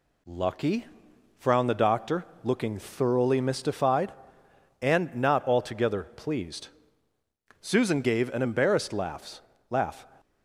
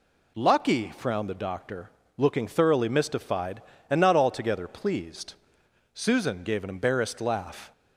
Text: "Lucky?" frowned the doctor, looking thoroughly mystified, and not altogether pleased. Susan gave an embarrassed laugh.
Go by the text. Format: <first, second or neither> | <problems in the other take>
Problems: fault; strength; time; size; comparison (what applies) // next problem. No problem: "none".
second | says "laugh" twice; at 9.6 s